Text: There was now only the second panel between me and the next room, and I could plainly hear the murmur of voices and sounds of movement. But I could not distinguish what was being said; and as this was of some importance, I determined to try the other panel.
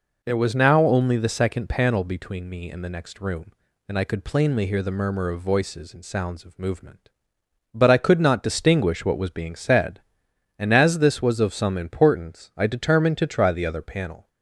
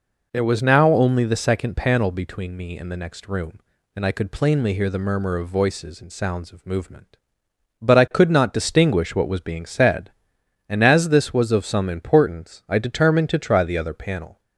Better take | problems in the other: neither | none

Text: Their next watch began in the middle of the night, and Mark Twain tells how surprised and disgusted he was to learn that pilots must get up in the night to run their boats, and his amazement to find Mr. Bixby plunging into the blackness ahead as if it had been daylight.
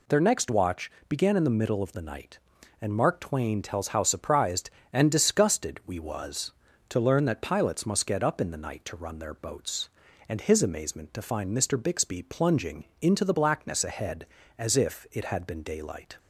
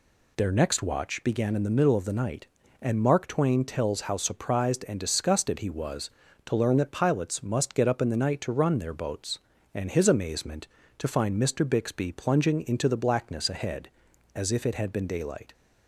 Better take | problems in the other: second | pauses between "watch" and "began"; slight; at 0.8 s; 0.18 s long // says "we" for "he"; at 5.8 s // pauses between "plunging" and "into"; slight; at 12.8 s; 0.16 s long

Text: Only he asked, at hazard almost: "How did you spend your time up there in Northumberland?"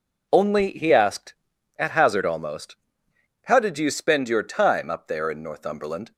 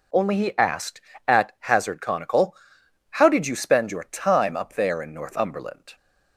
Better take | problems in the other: first | says "conical" for "almost"; at 2.0 s

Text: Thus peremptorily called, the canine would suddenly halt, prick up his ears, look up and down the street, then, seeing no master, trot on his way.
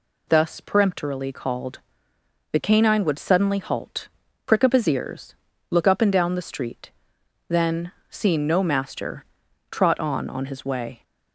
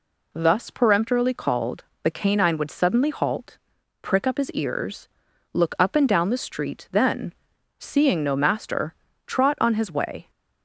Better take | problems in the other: second | says "on" twice; at 10.2 s

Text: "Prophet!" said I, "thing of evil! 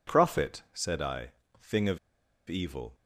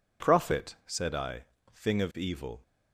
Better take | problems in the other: second | pauses between "of" and "evil"; noticeable; at 1.9 s; 0.50 s long

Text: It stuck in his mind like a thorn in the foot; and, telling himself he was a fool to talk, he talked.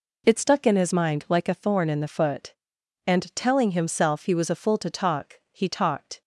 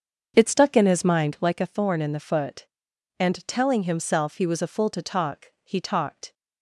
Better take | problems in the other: first | starts louder than the rest; until 1.5 s; 7 dB

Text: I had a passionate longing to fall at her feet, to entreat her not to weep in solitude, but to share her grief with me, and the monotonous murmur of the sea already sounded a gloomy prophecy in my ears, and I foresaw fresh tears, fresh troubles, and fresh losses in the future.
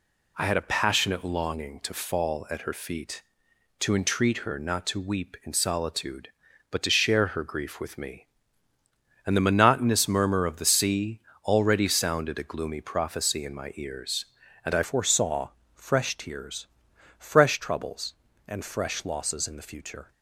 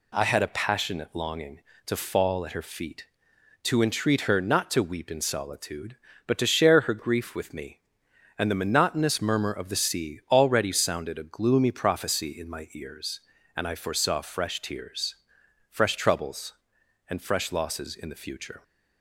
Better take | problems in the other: second | pauses between "sea" and "already"; slight; at 11.1 s; 0.24 s long // changes voice at "foresaw"; from 14.8 s on; 5.3 s long // pauses between "foresaw" and "fresh"; slight; at 15.4 s; 0.26 s long

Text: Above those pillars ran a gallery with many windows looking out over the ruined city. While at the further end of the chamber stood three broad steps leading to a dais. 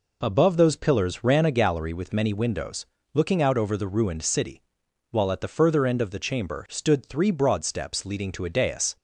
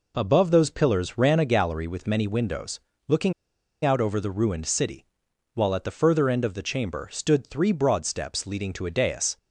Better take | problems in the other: first | pauses between "windows" and "looking"; slight; at 2.7 s; 0.28 s long; slight in the first // pauses between "looking" and "out"; noticeable; at 3.3 s; 0.52 s long

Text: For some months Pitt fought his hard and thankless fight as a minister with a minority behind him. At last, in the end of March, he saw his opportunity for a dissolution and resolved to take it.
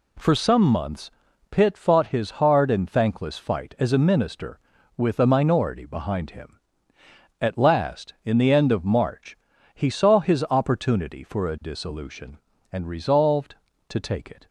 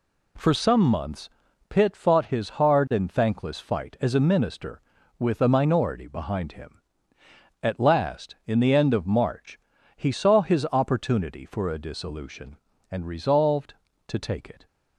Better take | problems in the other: neither | pauses between "months" and "Pitt"; the same in both

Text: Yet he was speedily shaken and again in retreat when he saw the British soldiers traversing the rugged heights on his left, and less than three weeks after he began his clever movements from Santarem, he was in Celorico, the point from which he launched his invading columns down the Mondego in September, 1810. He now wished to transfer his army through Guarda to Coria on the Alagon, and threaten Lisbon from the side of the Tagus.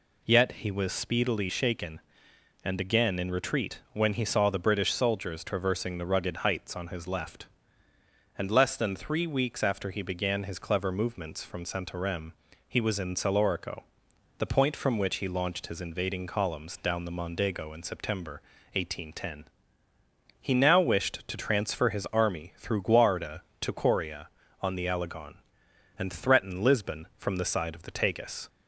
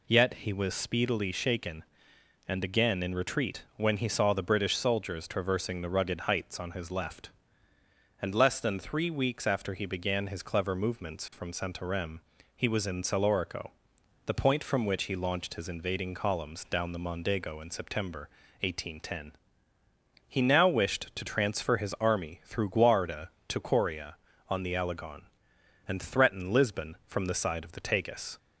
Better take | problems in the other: neither | pauses between "retreat" and "when"; slight; the same in both

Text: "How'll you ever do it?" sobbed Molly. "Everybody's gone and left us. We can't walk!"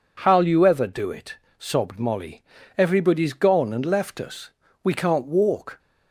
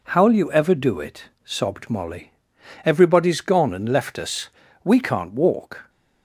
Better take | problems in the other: neither | none

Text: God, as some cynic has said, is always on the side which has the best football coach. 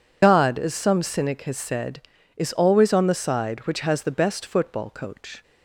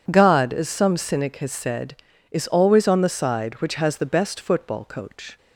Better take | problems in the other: second | loses the start of "God"; at 0.2 s; 90 ms

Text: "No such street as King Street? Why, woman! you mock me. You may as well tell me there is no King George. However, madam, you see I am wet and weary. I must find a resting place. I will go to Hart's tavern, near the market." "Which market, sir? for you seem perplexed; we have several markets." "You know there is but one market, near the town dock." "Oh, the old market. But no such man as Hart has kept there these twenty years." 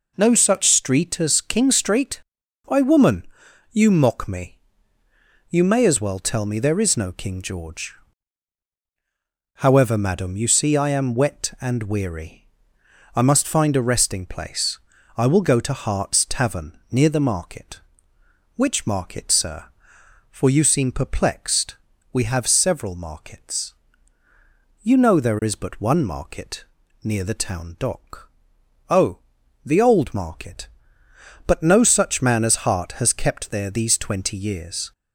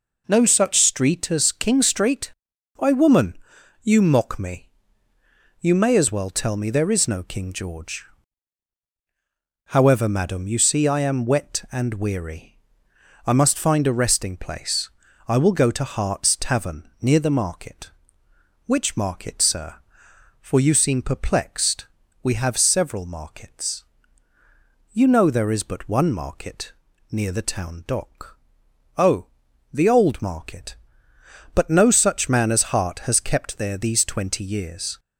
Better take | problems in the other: neither | none

